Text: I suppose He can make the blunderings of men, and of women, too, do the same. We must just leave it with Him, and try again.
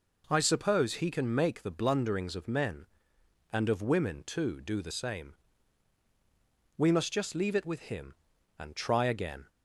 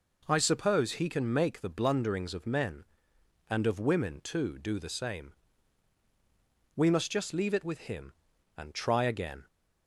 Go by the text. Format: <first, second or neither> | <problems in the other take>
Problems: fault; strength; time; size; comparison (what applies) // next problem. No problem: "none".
neither | none